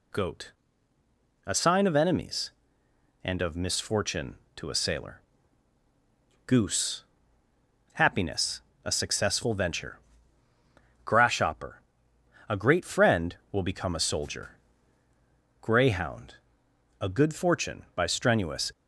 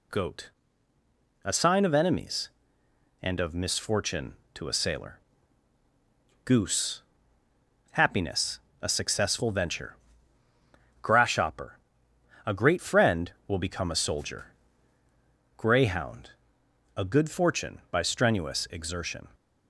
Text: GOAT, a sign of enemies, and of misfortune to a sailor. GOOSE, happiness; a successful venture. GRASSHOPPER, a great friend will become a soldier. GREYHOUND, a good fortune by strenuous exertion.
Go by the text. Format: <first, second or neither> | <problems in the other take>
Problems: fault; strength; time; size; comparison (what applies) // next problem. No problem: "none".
second | stops before "exertion"; at 18.7 s